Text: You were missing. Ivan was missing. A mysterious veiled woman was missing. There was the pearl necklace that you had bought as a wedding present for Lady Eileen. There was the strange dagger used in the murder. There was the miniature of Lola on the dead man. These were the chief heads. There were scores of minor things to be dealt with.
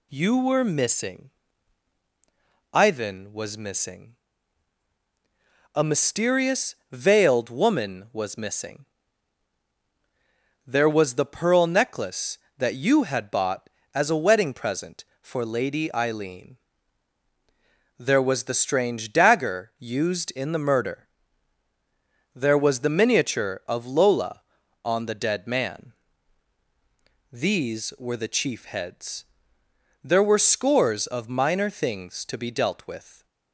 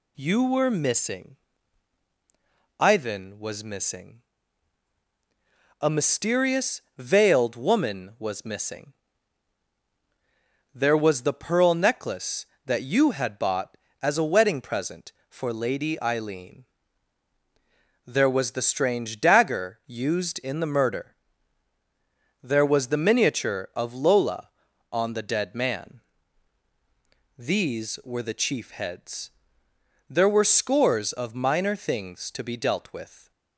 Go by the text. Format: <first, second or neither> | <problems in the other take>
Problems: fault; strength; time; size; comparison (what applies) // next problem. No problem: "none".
neither | pauses between "mysterious" and "veiled"; slight; the same in both